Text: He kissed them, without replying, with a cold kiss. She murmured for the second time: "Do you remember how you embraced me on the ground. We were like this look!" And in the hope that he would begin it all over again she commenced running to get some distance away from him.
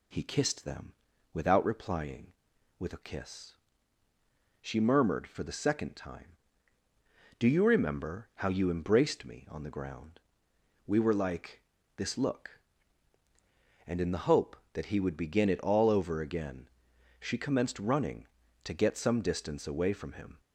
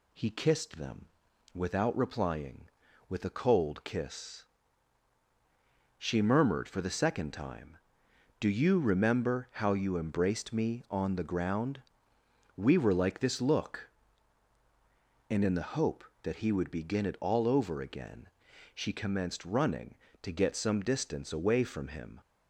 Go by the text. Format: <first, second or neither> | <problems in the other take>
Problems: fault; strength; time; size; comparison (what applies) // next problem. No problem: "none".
second | skips "cold"; at 3.0 s // pauses between "like" and "this"; slight; at 11.6 s; 0.36 s long // pauses between "again" and "she"; noticeable; at 16.6 s; 0.52 s long; also in the second